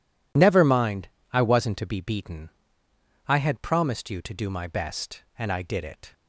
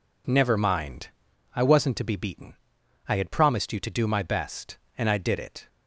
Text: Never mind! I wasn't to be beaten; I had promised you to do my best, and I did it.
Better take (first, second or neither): neither